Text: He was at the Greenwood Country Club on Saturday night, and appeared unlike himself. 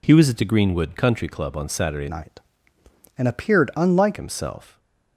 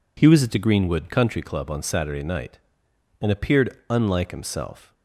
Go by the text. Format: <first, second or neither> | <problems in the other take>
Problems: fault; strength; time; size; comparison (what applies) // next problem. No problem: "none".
second | changes voice from "night" to "unlike"; from 2.0 to 4.1 s; 2.1 s long // stays silent after the last word; slight; from 4.6 s on; 0.5 s long